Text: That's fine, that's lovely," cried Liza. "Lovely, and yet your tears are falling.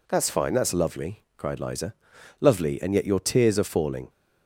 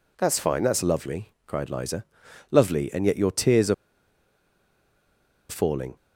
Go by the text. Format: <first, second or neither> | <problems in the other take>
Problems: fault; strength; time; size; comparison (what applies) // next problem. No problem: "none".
first | pauses between "are" and "falling"; strong; at 3.7 s; 1.7 s long